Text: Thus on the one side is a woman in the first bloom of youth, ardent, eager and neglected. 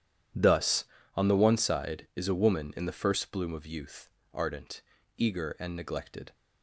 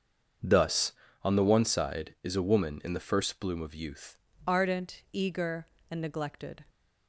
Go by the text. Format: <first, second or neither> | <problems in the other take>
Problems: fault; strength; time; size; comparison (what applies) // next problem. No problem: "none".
first | starts louder than the rest; until 1.7 s; 7 dB // changes voice at "ardent"; from 4.4 s on; 2.2 s long